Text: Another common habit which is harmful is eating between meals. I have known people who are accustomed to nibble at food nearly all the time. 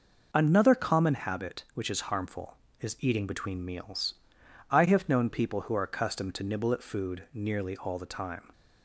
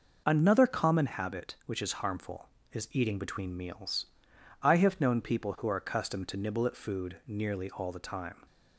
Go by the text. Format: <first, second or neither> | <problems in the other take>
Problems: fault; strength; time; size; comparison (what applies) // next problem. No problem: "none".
neither | none